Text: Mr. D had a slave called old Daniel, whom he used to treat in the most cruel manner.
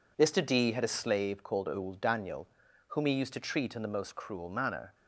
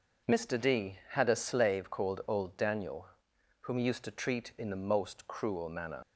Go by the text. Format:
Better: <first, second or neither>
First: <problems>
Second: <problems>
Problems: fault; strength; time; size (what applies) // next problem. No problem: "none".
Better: first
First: none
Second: leaves "manner" unfinished; at 6.0 s; 105 ms